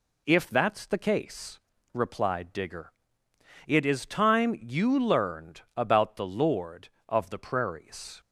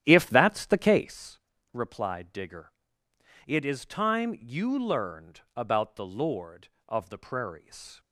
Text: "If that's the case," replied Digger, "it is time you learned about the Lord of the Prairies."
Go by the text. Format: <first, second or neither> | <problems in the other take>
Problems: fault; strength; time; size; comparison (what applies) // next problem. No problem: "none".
first | starts louder than the rest; strong; until 1.2 s; 11 dB